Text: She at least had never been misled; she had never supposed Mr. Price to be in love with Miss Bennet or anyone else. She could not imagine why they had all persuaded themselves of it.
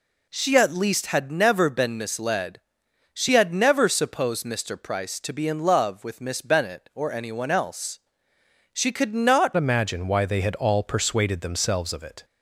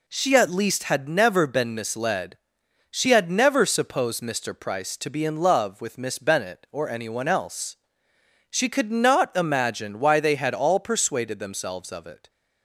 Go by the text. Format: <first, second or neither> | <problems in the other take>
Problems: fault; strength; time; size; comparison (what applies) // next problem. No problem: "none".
second | changes voice at "imagine"; from 9.5 s on; 2.7 s long